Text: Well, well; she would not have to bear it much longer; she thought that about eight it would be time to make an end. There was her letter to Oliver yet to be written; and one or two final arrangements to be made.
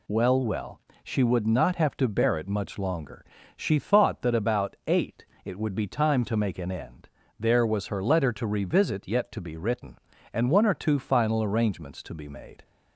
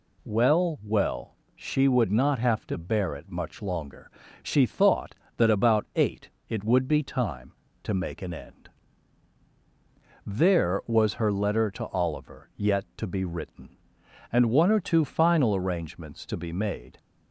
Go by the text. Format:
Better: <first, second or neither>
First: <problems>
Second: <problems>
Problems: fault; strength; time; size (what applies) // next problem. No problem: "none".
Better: second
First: pauses between "eight" and "it"; slight; at 5.2 s; 0.22 s long // says "Revisit" for "Oliver"; at 8.4 s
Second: pauses between "eight" and "it"; slight; at 6.2 s; 0.22 s long